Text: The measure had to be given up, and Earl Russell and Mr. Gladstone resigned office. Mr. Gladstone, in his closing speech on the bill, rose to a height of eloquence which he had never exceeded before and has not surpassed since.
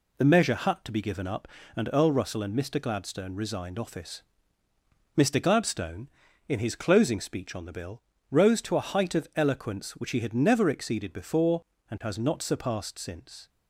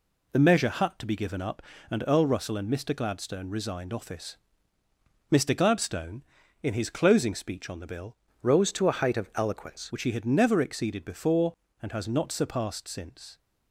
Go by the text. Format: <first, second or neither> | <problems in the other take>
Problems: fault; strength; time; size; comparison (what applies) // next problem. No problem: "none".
first | changes voice from "rose" to "eloquence"; from 8.4 to 9.9 s; 1.5 s long